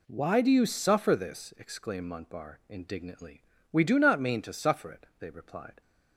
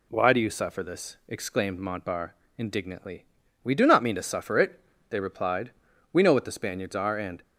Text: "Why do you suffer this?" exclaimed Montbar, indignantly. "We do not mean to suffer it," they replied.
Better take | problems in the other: first | goes on to say "We know what the Spaniards are and"; noticeable; from 6.1 s on; 1.3 s long

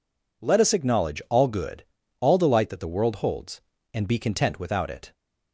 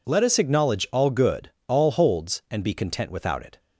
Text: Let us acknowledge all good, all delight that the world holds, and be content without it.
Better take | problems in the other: first | skips "delight that the world"; at 1.9 s

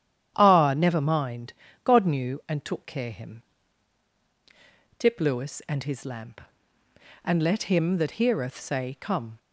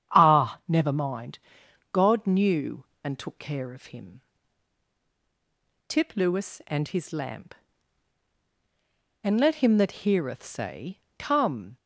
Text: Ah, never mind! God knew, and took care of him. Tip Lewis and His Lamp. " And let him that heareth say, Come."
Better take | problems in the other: second | starts louder than the rest; strong; until 1.3 s; 11 dB; strong in the second // skips "of"; at 3.1 s

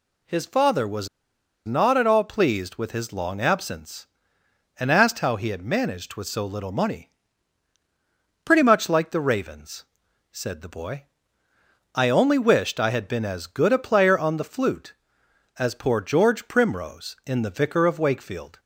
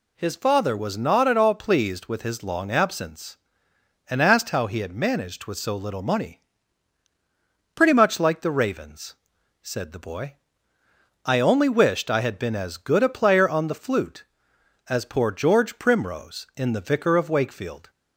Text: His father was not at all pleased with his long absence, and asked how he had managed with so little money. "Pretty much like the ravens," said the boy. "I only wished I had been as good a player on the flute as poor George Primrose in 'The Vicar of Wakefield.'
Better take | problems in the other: second | pauses between "was" and "not"; noticeable; at 1.0 s; 0.57 s long

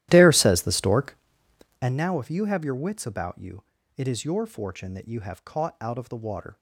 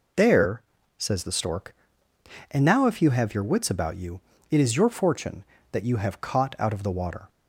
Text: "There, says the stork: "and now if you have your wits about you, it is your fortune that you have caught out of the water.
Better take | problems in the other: second | starts louder than the rest; strong; until 2.0 s; 14 dB

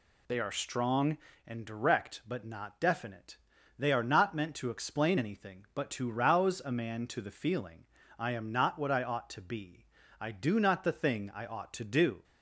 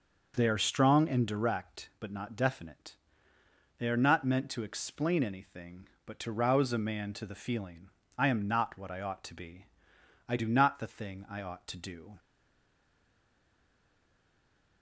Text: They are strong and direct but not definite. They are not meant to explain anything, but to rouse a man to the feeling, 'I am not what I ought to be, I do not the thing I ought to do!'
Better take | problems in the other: first | stays silent after the last word; strong; from 12.1 s on; 2.7 s long

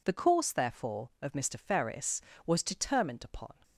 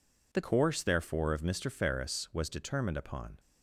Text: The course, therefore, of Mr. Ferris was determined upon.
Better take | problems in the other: first | changes voice at "course"; from 0.4 s on; 2.9 s long

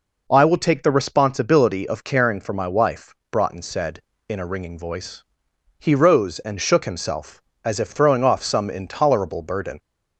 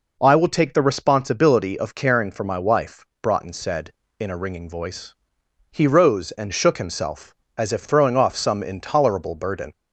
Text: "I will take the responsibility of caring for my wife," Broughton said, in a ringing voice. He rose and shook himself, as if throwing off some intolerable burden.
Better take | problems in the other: neither | none

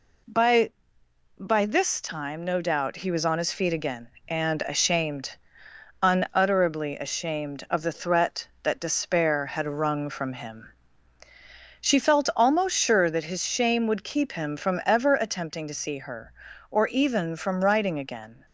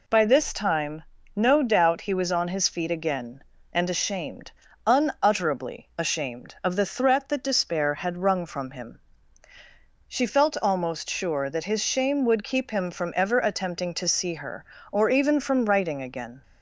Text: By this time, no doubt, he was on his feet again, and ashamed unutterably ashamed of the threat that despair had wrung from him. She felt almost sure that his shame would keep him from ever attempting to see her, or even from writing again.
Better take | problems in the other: second | says "By" twice; at 1.3 s // pauses between "ashamed" and "unutterably"; noticeable; at 5.3 s; 0.66 s long; slight in the second

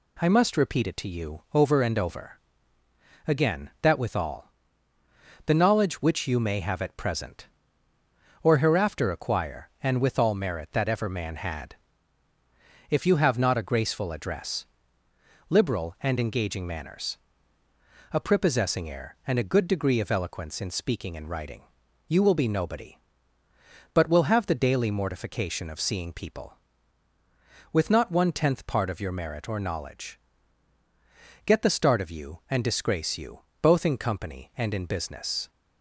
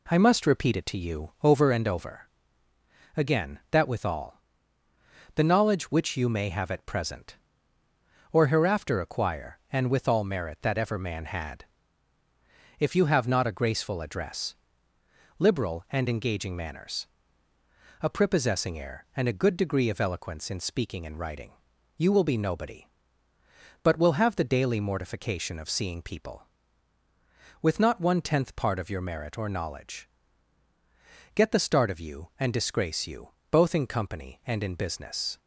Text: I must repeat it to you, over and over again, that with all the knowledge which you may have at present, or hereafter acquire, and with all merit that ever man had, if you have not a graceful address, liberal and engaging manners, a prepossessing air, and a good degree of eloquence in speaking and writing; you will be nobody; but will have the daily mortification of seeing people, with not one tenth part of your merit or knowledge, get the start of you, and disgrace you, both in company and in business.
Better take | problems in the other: first | starts louder than the rest; slight; until 1.9 s; 2 dB // pauses between "over" and "again"; noticeable; at 2.2 s; 0.96 s long; noticeable in the first // pauses between "all" and "the"; noticeable; at 4.4 s; 0.94 s long; noticeable in the first

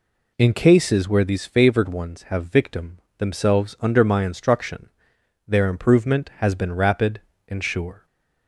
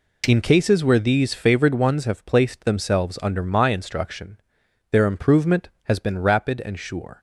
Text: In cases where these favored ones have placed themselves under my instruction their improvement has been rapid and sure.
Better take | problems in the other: second | says "victim" for "placed"; at 2.4 s // pauses between "instruction" and "their"; noticeable; at 4.8 s; 0.56 s long; noticeable in the second // stays silent after the last word; slight; from 7.9 s on; 0.5 s long

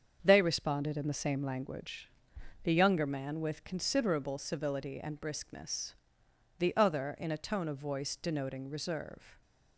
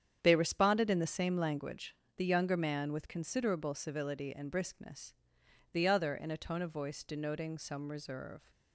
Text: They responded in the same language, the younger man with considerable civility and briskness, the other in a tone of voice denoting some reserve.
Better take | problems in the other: second | starts louder than the rest; until 1.2 s; 7 dB; strong in the second // skips "some"; at 8.6 s

